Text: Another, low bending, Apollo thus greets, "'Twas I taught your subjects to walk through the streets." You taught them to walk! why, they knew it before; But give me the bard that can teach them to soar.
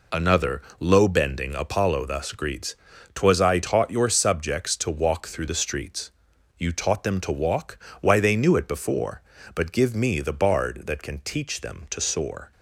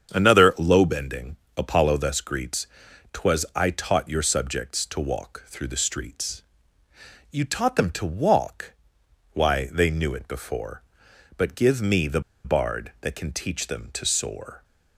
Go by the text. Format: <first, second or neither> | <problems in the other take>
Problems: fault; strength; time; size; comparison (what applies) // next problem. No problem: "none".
first | starts louder than the rest; strong; until 1.1 s; 7.5 dB // pauses between "the" and "bard"; slight; at 12.1 s; 0.24 s long